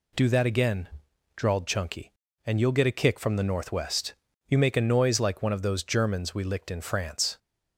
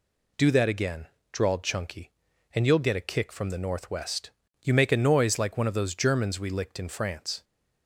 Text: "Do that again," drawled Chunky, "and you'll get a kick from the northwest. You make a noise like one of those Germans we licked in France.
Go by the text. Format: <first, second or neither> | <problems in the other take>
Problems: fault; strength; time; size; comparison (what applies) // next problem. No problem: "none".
neither | none